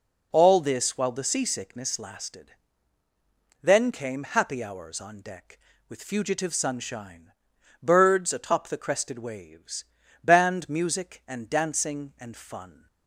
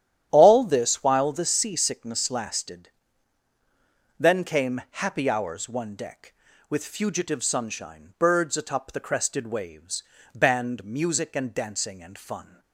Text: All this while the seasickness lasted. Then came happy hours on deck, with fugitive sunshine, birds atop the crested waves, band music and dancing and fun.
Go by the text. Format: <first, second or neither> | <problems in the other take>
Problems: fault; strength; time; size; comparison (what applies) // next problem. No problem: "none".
first | starts louder than the rest; strong; until 1.3 s; 11 dB // says "one" for "on"; at 5.6 s